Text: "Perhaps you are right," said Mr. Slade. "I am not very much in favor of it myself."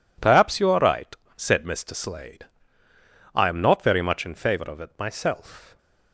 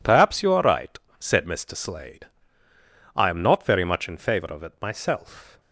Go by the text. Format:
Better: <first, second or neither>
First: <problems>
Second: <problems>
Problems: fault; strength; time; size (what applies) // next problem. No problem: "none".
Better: neither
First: none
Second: none